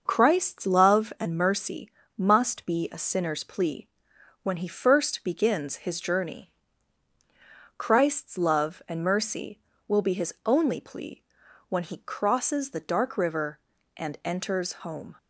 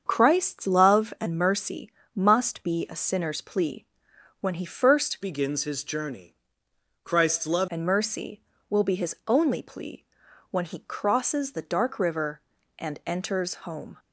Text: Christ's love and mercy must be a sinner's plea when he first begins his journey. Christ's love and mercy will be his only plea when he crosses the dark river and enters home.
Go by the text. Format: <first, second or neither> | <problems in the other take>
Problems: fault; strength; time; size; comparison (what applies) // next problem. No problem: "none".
first | starts louder than the rest; strong; until 1.0 s; 7 dB; noticeable in the first // pauses between "mercy" and "must"; slight; at 1.9 s; 0.24 s long; slight in the first // pauses between "plea" and "when"; noticeable; at 3.8 s; 0.54 s long; noticeable in the first // changes voice from "begins" to "love"; from 5.2 to 7.6 s; 2.4 s long // pauses between "plea" and "when"; noticeable; at 10.0 s; 0.48 s long; noticeable in the first